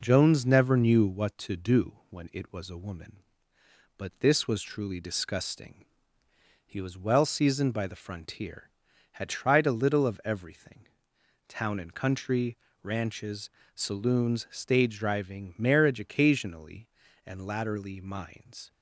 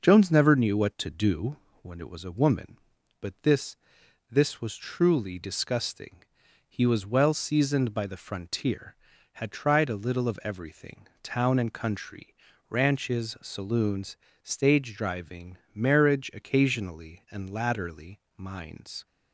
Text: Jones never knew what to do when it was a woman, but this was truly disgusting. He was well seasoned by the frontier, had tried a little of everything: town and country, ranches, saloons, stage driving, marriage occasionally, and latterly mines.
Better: first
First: none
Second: pauses between "do" and "when"; slight; at 1.5 s; 0.26 s long // says "this" twice; at 4.3 s // pauses between "latterly" and "mines"; slight; at 18.1 s; 0.18 s long

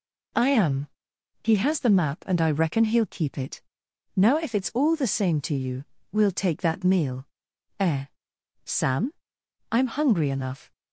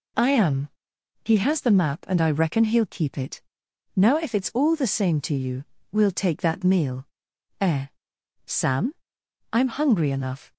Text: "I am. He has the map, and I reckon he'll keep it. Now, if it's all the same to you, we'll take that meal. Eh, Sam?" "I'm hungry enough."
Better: neither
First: none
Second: none

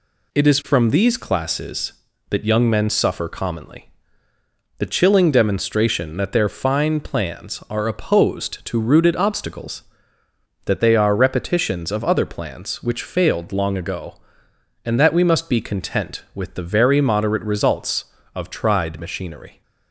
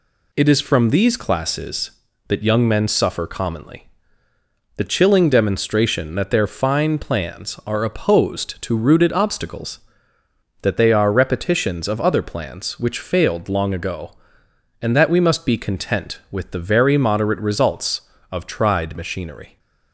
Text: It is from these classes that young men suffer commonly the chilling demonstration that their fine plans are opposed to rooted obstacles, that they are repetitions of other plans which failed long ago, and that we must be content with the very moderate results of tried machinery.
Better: neither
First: pauses between "commonly" and "the"; noticeable; at 3.9 s; 0.88 s long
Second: pauses between "commonly" and "the"; noticeable; at 3.8 s; 0.88 s long

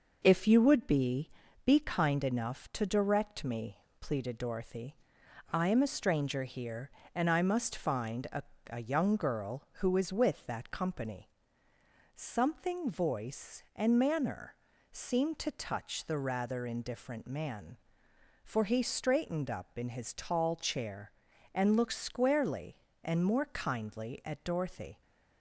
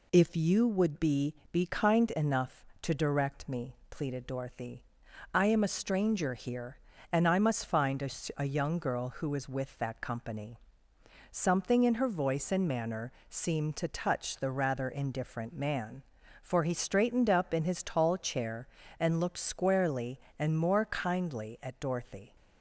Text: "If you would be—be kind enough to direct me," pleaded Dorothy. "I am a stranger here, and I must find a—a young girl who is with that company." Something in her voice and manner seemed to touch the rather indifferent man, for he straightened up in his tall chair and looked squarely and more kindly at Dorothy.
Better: second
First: skips "in her"; at 12.8 s // pauses between "manner" and "seemed"; at 14.5 s; 0.38 s long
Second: pauses between "manner" and "seemed"; slight; at 13.1 s; 0.18 s long

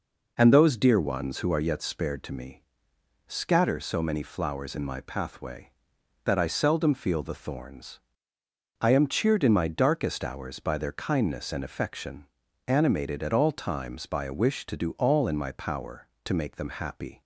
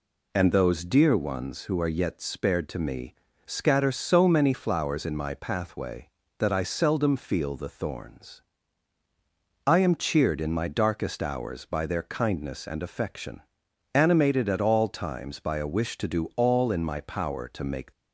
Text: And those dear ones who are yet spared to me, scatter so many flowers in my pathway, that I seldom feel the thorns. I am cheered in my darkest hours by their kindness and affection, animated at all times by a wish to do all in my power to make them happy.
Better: first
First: none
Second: stops before "them happy"; at 17.9 s

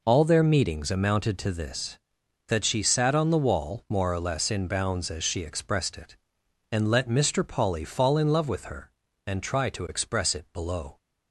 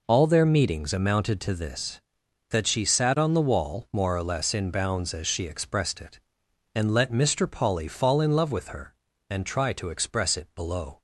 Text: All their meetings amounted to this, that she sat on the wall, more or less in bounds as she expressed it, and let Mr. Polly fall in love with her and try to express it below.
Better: neither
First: none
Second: none

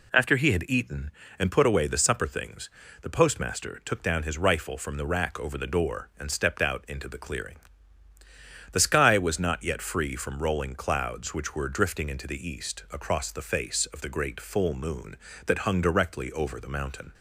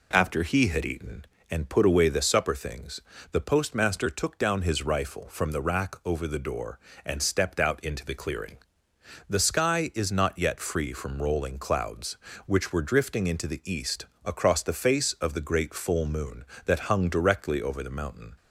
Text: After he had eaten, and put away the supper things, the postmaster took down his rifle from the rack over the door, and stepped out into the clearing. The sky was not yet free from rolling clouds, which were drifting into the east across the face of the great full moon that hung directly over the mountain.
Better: first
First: none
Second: says "is" for "was"; at 9.9 s // pauses between "east" and "across"; slight; at 14.0 s; 0.18 s long

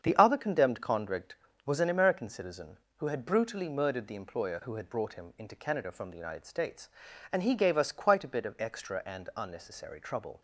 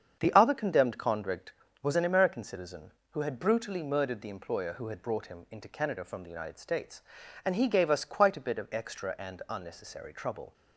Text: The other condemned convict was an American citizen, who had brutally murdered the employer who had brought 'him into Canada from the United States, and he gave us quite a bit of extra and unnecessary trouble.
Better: neither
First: starts louder than the rest; strong; until 1.0 s; 7.5 dB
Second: starts louder than the rest; strong; until 1.2 s; 7.5 dB

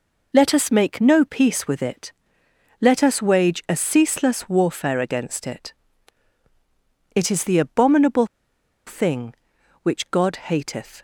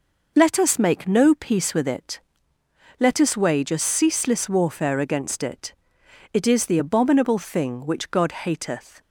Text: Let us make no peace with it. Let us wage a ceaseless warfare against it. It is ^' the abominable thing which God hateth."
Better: second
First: pauses between "abominable" and "thing"; noticeable; at 8.2 s; 0.60 s long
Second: none

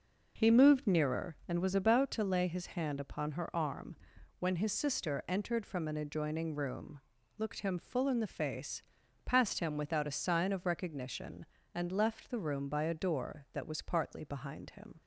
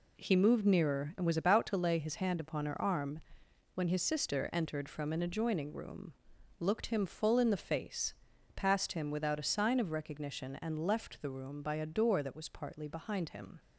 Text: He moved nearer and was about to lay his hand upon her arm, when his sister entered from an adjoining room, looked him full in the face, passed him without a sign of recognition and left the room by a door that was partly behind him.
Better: neither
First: none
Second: none

